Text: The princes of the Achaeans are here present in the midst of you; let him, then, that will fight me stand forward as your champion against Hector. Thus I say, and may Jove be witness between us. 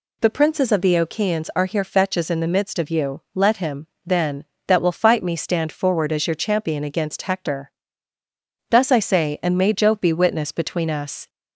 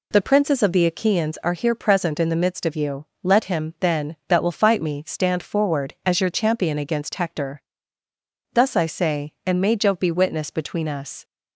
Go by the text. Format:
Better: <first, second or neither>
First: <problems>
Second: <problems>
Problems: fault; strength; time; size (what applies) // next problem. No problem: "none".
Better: second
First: says "fetches" for "present"; at 1.8 s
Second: none